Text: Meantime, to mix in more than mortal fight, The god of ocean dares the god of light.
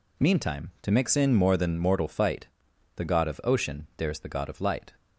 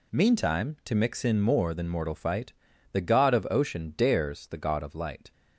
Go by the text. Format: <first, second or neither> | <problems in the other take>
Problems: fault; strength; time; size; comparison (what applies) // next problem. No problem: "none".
neither | none